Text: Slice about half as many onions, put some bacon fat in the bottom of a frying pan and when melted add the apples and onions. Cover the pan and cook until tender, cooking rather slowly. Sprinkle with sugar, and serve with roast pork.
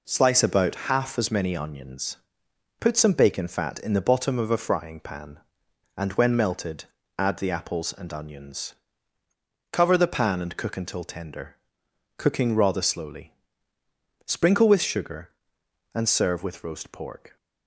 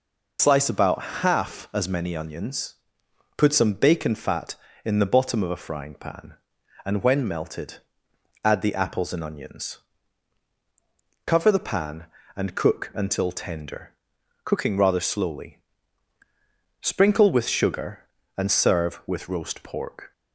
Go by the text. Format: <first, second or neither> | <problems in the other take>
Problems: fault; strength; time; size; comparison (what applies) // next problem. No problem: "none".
first | loses the start of "Slice"; at 0.3 s; 85 ms // pauses between "about" and "half"; slight; at 1.0 s; 0.20 s long // pauses between "melted" and "add"; noticeable; at 7.7 s; 0.66 s long; slight in the first